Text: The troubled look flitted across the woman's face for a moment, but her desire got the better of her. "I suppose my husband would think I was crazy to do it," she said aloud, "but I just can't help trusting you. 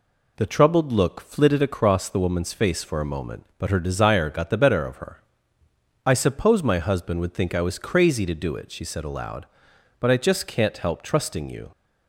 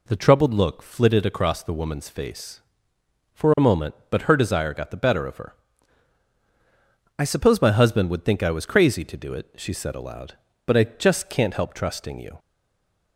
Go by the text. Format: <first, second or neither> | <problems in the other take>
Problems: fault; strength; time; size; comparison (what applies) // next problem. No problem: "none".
first | stays silent after the last word; slight; from 12.3 s on; 0.8 s long